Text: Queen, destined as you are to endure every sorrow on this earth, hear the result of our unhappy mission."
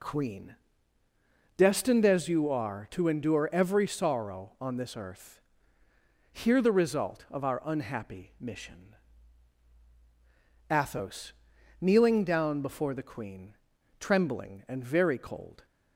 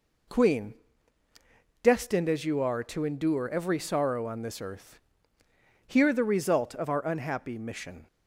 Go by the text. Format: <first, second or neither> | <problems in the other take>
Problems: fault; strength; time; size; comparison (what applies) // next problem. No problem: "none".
second | goes on to say "Athos kneeling down before the queen trembling and very cold"; strong; from 10.7 s on; 4.9 s long